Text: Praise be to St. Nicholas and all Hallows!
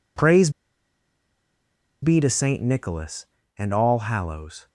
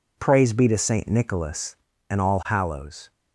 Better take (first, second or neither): second